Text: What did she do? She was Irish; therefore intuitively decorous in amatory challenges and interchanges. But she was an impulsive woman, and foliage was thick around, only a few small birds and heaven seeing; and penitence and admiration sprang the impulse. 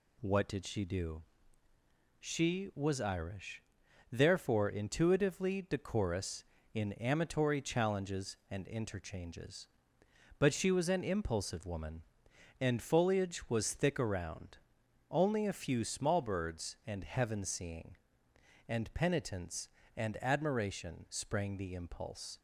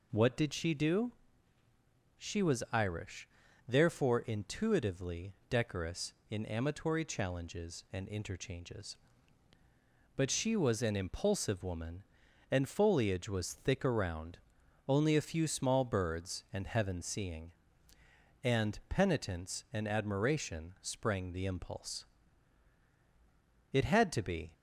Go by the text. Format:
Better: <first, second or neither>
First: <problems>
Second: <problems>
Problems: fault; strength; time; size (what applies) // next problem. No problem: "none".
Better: first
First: none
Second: pauses between "intuitively" and "decorous"; slight; at 5.3 s; 0.16 s long // goes on to say "It had to be"; noticeable; from 23.7 s on; 0.80 s long